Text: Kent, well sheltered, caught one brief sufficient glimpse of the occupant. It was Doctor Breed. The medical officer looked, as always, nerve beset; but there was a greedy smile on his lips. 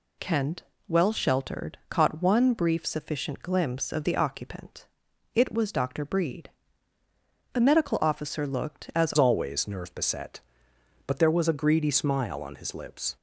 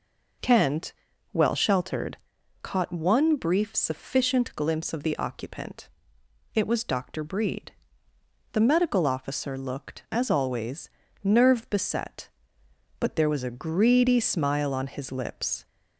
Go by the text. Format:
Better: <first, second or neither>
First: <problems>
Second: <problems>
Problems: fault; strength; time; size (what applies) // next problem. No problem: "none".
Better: second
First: changes voice at "always"; from 9.1 s on; 4.0 s long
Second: none